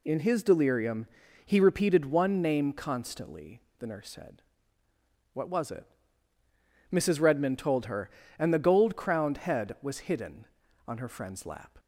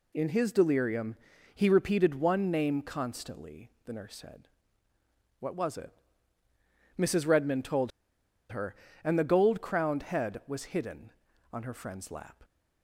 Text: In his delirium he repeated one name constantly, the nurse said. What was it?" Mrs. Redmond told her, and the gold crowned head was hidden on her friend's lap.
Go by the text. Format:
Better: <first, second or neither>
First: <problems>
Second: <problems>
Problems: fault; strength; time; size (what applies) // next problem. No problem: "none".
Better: first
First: pauses between "delirium" and "he"; at 1.0 s; 0.40 s long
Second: pauses between "delirium" and "he"; at 1.1 s; 0.40 s long // pauses between "told" and "her"; noticeable; at 7.9 s; 0.61 s long